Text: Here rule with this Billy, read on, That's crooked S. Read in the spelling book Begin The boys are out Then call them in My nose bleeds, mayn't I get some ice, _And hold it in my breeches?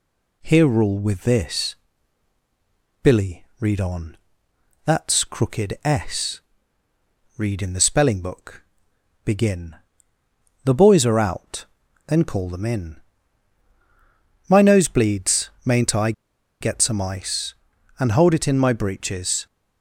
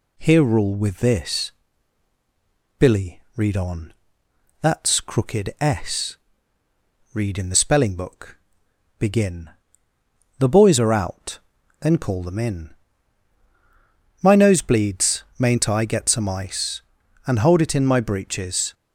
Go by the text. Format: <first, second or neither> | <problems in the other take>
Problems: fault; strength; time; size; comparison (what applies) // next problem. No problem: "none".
second | pauses between "this" and "Billy"; strong; at 1.7 s; 1.2 s long; strong in the second // pauses between "book" and "Begin"; noticeable; at 8.6 s; 0.62 s long; noticeable in the second // pauses between "Begin" and "The"; noticeable; at 9.7 s; 0.88 s long; noticeable in the second // pauses between "out" and "Then"; at 11.6 s; 0.42 s long; also in the second // pauses between "in" and "My"; strong; at 12.9 s; 1.4 s long; strong in the second // pauses between "I" and "get"; noticeable; at 16.1 s; 0.49 s long